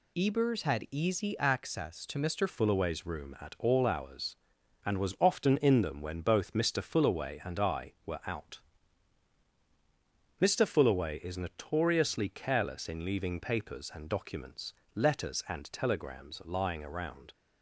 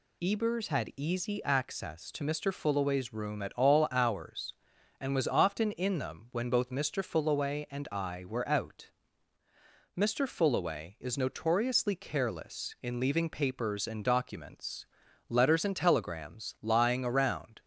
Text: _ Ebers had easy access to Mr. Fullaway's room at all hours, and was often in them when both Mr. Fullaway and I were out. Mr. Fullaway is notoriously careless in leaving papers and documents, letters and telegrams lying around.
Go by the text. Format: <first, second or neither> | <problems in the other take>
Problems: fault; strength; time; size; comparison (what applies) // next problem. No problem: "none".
second | changes voice at "Fullaway's"; from 2.4 s on; 14.9 s long